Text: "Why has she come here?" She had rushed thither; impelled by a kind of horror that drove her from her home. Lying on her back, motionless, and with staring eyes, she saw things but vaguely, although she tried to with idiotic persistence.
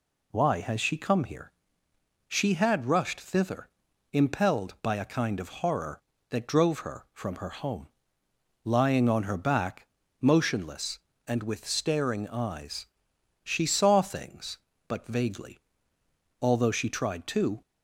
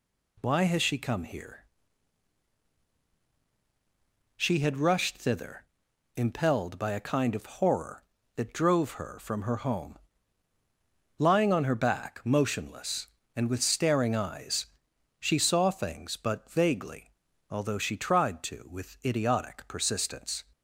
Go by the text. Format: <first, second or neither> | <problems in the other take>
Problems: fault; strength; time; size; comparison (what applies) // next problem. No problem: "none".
second | stops before "with idiotic persistence"; at 17.6 s